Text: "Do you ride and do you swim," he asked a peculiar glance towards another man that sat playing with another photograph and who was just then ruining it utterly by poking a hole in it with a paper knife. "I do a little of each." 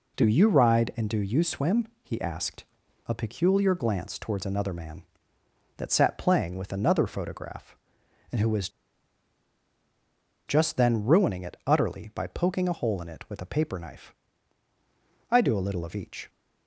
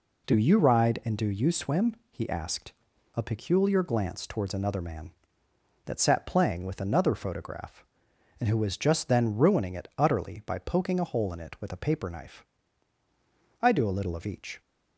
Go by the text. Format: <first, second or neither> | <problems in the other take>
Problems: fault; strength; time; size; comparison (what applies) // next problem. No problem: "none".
second | pauses between "asked" and "a"; at 2.6 s; 0.44 s long; also in the second // pauses between "was" and "just"; strong; at 8.6 s; 1.7 s long